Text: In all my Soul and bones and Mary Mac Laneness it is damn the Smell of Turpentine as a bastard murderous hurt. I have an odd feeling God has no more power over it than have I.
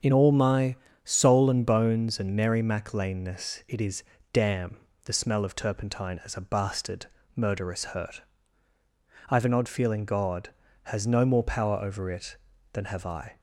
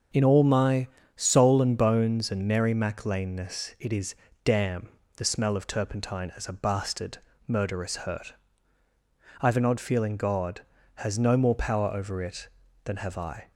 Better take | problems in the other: neither | starts louder than the rest; the same in both // pauses between "my" and "Soul"; slight; the same in both // pauses between "is" and "damn"; slight; the same in both // pauses between "damn" and "the"; slight; the same in both // pauses between "bastard" and "murderous"; slight; the same in both

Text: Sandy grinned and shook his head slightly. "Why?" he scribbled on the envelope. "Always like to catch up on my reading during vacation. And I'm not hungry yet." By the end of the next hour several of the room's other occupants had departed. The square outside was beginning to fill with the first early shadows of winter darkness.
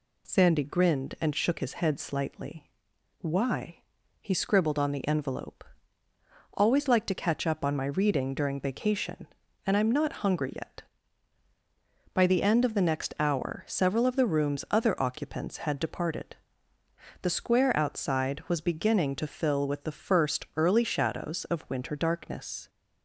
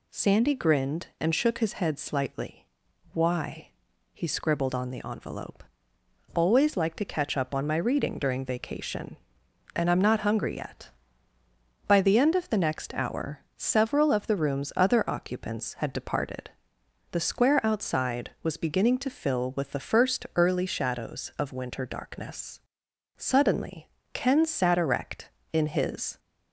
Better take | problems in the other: first | pauses between "hour" and "several"; slight; at 13.4 s; 0.16 s long // goes on to say "Suddenly Ken sat erect in his"; strong; from 23.1 s on; 3.0 s long

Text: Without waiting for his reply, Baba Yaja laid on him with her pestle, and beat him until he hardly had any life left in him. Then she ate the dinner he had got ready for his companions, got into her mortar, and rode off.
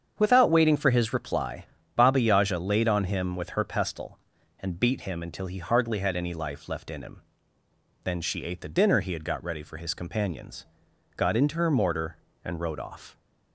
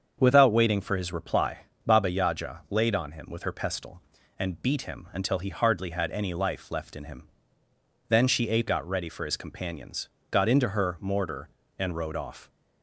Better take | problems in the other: first | starts louder than the rest; until 1.2 s; 7 dB; strong in the first // skips "the dinner he had"; at 8.6 s

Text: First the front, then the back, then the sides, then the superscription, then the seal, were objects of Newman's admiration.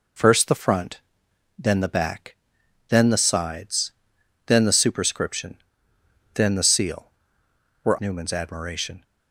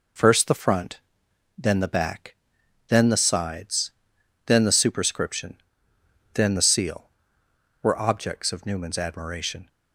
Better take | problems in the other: second | skips "objects of"; at 7.9 s

